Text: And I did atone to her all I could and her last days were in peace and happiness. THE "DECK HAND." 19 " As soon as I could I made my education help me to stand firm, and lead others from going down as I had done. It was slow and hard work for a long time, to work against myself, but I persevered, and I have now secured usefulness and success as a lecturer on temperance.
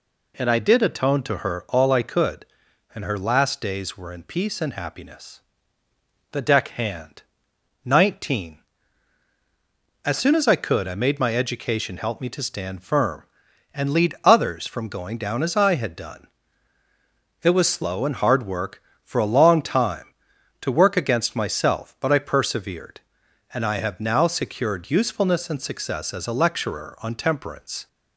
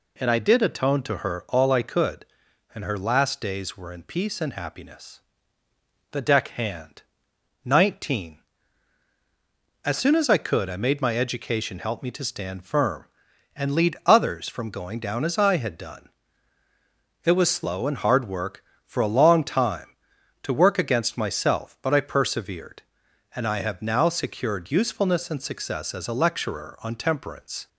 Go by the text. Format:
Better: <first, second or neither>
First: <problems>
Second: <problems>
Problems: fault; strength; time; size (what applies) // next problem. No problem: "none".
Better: neither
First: none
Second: none